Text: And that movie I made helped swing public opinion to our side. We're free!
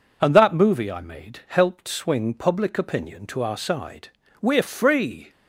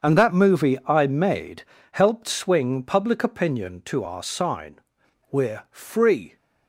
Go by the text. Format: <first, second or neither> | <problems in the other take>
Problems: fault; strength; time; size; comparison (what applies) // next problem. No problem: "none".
first | starts louder than the rest; until 1.1 s; 7 dB // pauses between "made" and "helped"; slight; at 1.6 s; 0.30 s long // says "sign" for "side"; at 4.2 s